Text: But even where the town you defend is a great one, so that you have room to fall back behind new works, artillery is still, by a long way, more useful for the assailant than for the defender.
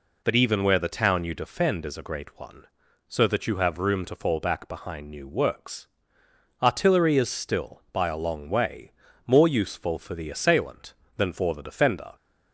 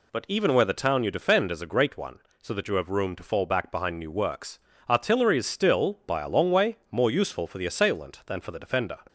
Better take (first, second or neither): neither